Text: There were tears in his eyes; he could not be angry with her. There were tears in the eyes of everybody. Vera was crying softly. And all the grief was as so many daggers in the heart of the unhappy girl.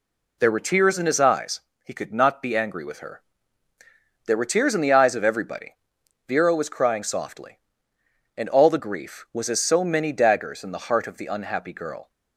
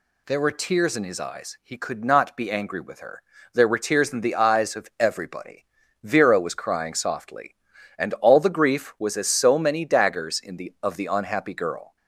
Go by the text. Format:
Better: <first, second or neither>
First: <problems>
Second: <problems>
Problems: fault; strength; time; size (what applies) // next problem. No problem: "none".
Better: first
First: none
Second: skips "heart"; at 10.7 s